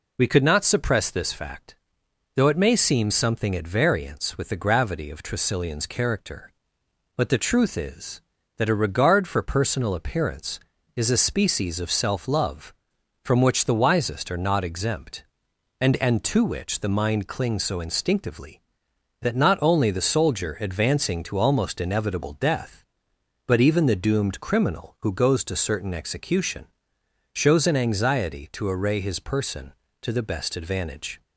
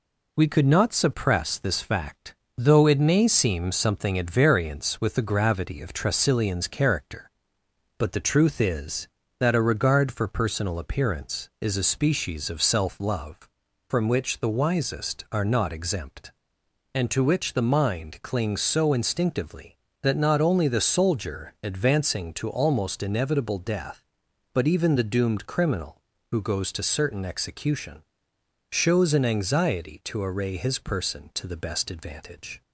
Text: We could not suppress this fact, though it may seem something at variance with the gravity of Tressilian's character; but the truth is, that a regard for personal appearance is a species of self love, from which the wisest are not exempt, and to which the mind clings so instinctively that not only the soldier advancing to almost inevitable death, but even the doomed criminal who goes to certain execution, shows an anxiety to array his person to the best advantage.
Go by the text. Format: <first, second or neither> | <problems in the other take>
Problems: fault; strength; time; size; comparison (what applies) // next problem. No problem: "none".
second | says "and" twice; at 15.9 s